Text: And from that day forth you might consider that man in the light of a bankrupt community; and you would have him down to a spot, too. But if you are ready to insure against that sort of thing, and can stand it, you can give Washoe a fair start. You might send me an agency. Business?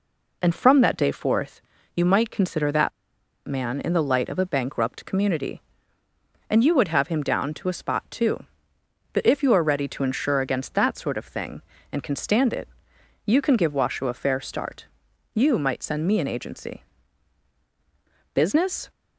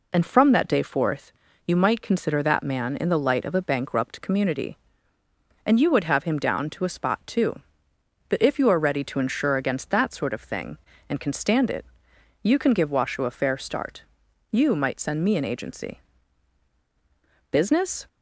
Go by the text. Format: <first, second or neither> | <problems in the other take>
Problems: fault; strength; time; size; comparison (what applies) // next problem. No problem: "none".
second | pauses between "forth" and "you"; slight; at 1.6 s; 0.34 s long; slight in the second // pauses between "that" and "man"; noticeable; at 2.9 s; 0.57 s long